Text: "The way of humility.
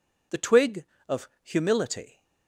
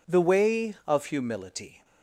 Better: second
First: says "twig" for "way"; at 0.3 s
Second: none

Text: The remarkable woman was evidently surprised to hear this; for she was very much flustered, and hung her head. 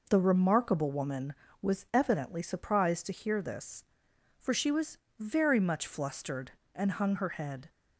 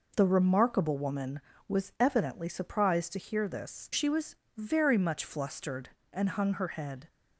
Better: first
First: pauses between "was" and "very"; slight; at 4.9 s; 0.20 s long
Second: skips "for"; at 3.9 s // pauses between "was" and "very"; slight; at 4.3 s; 0.20 s long

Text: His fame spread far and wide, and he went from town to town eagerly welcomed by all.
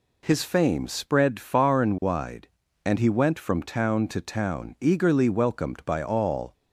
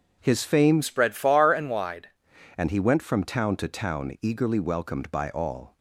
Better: first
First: none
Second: changes voice from "spread" to "wide"; from 0.8 to 2.0 s; 1.2 s long

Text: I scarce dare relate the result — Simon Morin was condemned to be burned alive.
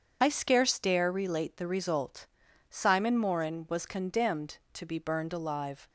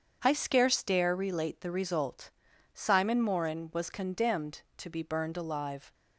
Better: second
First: loses the start of "I"; at 0.2 s; 30 ms // starts louder than the rest; until 1.2 s; 7 dB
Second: starts louder than the rest; strong; until 1.2 s; 7 dB

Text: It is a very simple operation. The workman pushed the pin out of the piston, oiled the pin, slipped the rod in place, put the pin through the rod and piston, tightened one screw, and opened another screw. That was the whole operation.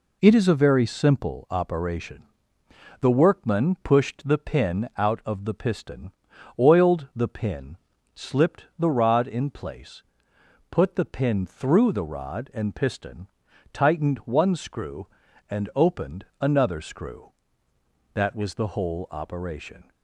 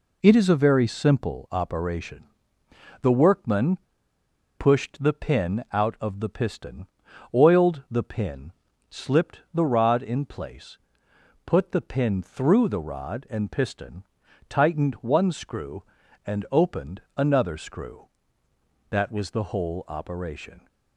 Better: first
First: pauses between "opened" and "another"; slight; at 16.2 s; 0.16 s long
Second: pauses between "workman" and "pushed"; noticeable; at 3.7 s; 0.83 s long // pauses between "opened" and "another"; slight; at 17.0 s; 0.16 s long

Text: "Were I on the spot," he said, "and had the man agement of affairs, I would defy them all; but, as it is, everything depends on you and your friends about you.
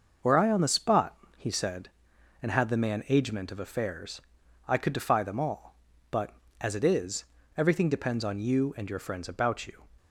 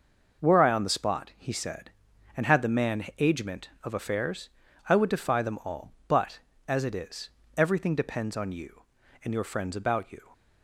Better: second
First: starts louder than the rest; until 1.4 s; 6 dB // says "could" for "would"; at 4.7 s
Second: none

